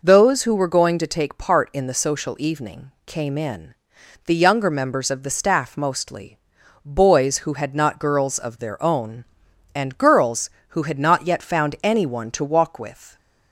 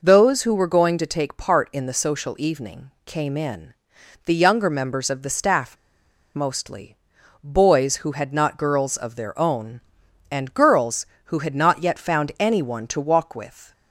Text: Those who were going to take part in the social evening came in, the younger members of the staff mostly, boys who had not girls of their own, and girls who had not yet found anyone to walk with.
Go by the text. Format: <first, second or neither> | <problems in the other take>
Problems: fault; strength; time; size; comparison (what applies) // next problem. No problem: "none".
first | pauses between "evening" and "came"; slight; at 2.8 s; 0.16 s long; slight in the first // pauses between "staff" and "mostly"; noticeable; at 5.7 s; 0.59 s long